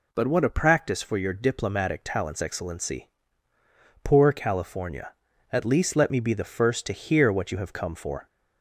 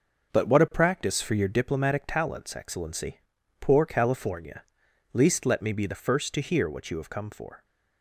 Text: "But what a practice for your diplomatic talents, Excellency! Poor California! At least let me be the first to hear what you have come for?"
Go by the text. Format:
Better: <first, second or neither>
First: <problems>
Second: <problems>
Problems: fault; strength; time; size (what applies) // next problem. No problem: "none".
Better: first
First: none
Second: starts louder than the rest; noticeable; until 1.3 s; 6 dB // skips "At"; at 4.8 s